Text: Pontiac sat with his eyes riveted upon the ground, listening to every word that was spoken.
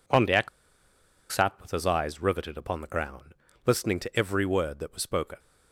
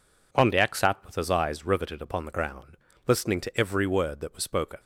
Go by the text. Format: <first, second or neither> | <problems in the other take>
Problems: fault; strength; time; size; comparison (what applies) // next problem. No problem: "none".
second | pauses between "Pontiac" and "sat"; noticeable; at 0.4 s; 0.83 s long